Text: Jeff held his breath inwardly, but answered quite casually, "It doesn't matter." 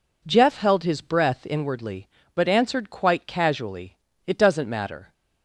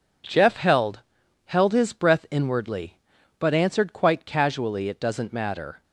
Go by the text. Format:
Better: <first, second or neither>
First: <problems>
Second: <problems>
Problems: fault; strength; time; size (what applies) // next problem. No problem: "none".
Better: first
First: none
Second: says "held" twice; at 1.4 s